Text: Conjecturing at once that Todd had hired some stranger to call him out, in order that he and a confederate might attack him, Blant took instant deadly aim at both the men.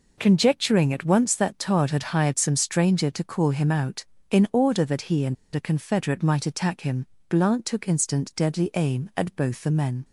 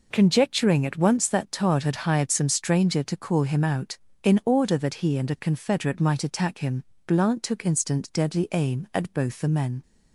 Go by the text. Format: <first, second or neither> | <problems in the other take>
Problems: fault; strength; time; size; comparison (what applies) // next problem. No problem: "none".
second | pauses between "and" and "a"; slight; at 5.3 s; 0.19 s long